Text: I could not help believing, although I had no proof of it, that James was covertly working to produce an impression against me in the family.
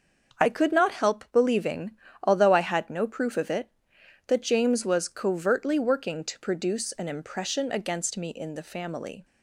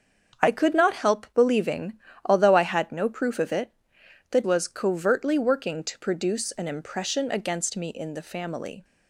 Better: first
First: starts louder than the rest; until 1.4 s; 7 dB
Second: starts louder than the rest; strong; until 1.4 s; 7.5 dB // skips "James"; at 4.4 s

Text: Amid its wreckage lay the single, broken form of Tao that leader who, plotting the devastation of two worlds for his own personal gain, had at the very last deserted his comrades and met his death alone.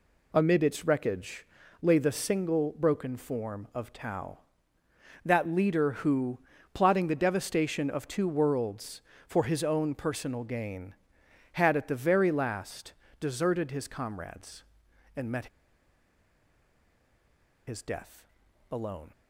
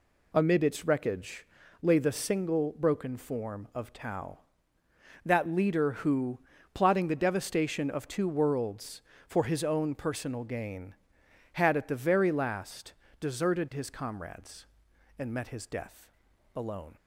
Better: second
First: pauses between "wreckage" and "lay"; slight; at 1.4 s; 0.36 s long // pauses between "last" and "deserted"; slight; at 12.9 s; 0.28 s long // pauses between "met" and "his"; strong; at 15.4 s; 2.2 s long // pauses between "death" and "alone"; at 18.2 s; 0.44 s long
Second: pauses between "wreckage" and "lay"; slight; at 1.4 s; 0.36 s long // pauses between "last" and "deserted"; slight; at 12.9 s; 0.28 s long // pauses between "death" and "alone"; at 16.1 s; 0.44 s long

